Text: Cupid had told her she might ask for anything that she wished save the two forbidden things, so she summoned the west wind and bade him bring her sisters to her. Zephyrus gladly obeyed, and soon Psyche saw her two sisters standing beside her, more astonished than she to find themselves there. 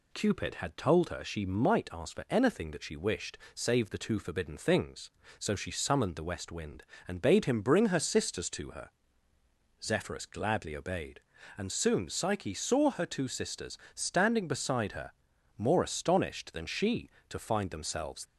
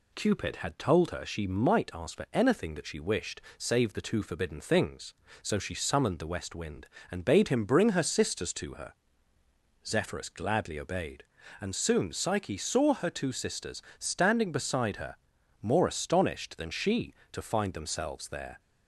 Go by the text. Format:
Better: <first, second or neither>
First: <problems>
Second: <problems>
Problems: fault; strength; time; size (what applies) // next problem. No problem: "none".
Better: second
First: pauses between "wished" and "save"; slight; at 3.3 s; 0.16 s long // pauses between "sisters" and "standing"; slight; at 13.7 s; 0.16 s long // stops before "there"; at 18.2 s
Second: pauses between "wished" and "save"; slight; at 3.4 s; 0.16 s long // pauses between "sisters" and "standing"; slight; at 13.8 s; 0.16 s long